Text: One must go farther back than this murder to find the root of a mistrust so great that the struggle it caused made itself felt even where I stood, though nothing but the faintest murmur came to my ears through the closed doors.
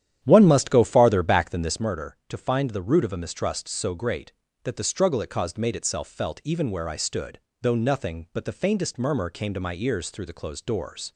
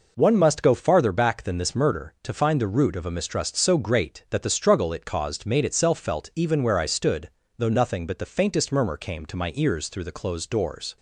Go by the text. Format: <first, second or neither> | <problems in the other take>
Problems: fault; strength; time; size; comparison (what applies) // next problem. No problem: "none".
second | starts louder than the rest; strong; until 1.9 s; 10.5 dB